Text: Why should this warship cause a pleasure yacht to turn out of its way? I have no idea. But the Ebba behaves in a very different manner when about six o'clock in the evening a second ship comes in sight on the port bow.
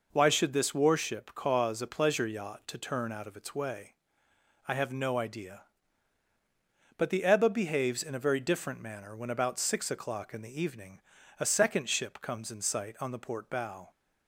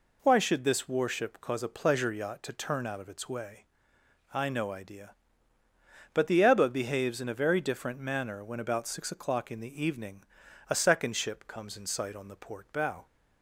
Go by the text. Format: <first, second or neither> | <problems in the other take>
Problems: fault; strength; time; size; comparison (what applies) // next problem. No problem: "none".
first | skips "have"; at 4.4 s // pauses between "evening" and "a"; at 10.2 s; 0.44 s long; also in the first